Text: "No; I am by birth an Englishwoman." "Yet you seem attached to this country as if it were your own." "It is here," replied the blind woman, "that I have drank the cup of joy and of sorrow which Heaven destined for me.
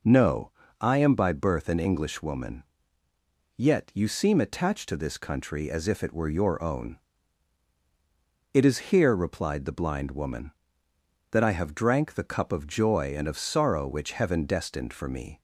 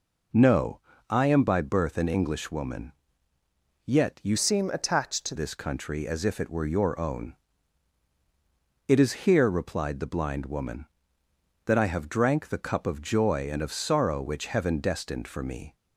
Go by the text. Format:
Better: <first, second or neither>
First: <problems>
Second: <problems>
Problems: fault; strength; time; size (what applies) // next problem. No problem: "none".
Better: first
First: none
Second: changes voice from "seem" to "to"; from 4.3 to 5.3 s; 1.0 s long